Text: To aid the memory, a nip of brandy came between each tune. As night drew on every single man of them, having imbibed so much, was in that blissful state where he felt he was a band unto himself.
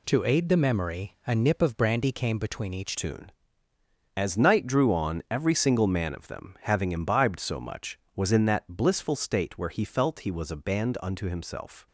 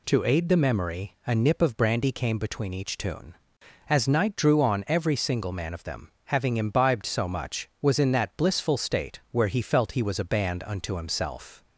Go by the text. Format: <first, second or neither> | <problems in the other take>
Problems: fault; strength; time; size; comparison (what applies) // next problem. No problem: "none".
second | changes voice at "tune"; from 2.9 s on; 8.9 s long